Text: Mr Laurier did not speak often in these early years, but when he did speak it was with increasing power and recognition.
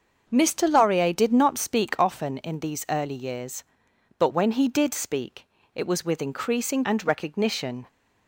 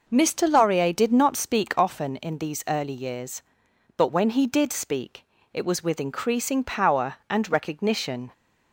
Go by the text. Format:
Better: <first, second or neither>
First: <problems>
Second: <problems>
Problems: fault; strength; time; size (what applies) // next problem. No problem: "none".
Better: second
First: starts louder than the rest; until 1.2 s; 6.5 dB // pauses between "speak" and "it"; slight; at 5.4 s; 0.28 s long // skips "power"; at 6.8 s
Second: pauses between "speak" and "it"; slight; at 5.2 s; 0.28 s long